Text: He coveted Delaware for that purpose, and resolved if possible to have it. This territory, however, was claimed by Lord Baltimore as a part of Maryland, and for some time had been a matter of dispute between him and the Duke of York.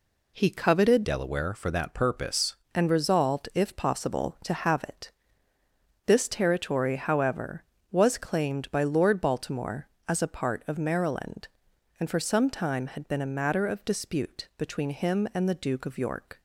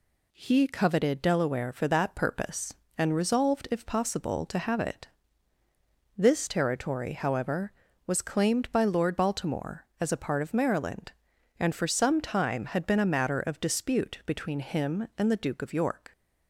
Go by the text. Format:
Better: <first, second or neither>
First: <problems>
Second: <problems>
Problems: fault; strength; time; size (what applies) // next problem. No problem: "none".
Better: second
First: changes voice from "Delaware" to "purpose"; from 1.0 to 2.5 s; 1.5 s long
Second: none